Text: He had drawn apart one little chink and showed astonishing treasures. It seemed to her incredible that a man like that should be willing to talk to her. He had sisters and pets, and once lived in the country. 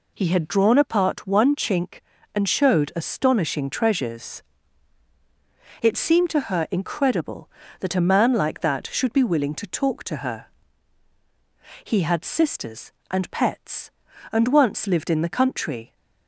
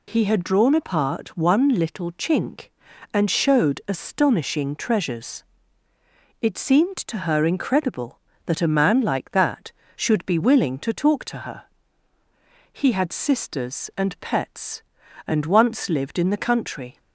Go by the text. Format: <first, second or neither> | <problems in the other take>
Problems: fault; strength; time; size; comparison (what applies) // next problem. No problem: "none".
second | skips "little"; at 1.5 s